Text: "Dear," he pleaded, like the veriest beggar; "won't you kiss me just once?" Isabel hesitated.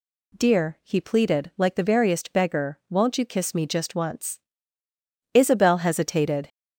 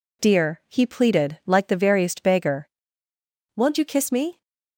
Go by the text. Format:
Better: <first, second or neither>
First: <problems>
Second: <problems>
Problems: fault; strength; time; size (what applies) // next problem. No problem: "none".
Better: first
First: none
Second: stops before "just once Isabel hesitated"; at 4.4 s